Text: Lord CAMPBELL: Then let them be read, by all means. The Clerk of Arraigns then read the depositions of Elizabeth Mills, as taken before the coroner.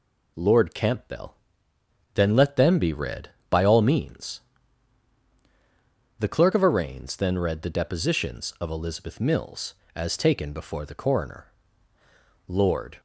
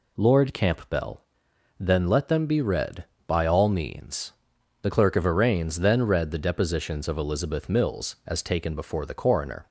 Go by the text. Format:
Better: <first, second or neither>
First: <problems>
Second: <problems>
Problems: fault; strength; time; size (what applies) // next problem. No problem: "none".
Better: second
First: goes on to say "Lord"; from 12.4 s on; 0.54 s long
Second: none